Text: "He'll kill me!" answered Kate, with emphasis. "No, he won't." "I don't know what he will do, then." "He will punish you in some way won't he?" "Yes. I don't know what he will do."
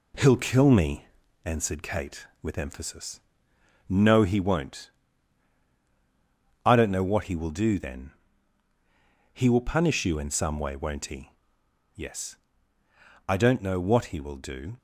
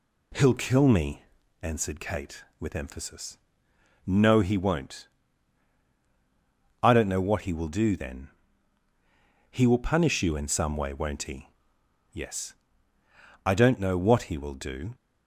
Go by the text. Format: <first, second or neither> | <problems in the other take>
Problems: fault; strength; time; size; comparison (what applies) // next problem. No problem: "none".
second | gets quieter; throughout; 3.5 dB